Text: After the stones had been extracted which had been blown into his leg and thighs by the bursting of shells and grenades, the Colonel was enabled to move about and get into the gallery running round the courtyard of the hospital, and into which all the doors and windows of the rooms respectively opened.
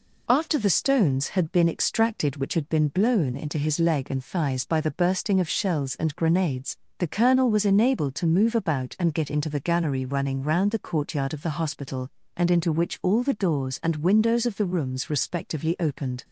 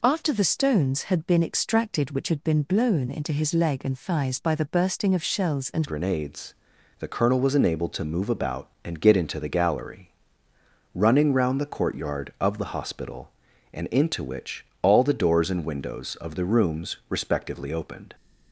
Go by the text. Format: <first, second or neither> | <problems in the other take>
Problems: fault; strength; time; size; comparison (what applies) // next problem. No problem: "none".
first | changes voice at "grenades"; from 5.8 s on; 12.3 s long // pauses between "gallery" and "running"; noticeable; at 10.1 s; 0.84 s long // pauses between "which" and "all"; slight; at 14.6 s; 0.16 s long